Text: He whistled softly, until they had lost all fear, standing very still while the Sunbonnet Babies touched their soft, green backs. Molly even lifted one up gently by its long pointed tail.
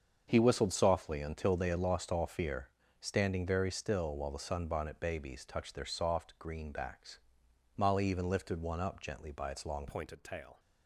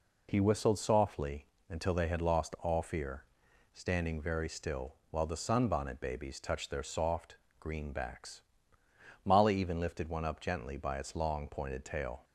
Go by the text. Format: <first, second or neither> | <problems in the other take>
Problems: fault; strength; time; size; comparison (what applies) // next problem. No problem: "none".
second | starts louder than the rest; until 1.2 s; 7 dB // changes voice at "pointed"; from 9.8 s on; 0.7 s long